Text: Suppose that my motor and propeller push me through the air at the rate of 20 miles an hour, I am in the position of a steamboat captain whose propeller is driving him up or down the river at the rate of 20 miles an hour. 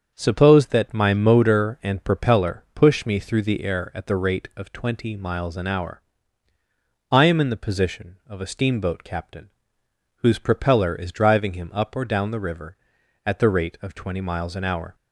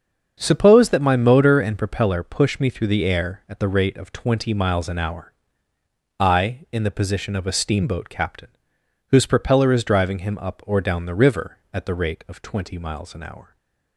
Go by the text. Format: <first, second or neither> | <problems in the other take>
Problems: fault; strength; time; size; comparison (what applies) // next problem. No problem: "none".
first | starts louder than the rest; until 1.4 s; 7 dB; also in the first // skips "am"; at 6.6 s // pauses between "captain" and "whose"; noticeable; at 8.5 s; 0.58 s long; noticeable in the first // stays silent after the last word; slight; from 13.4 s on; 0.5 s long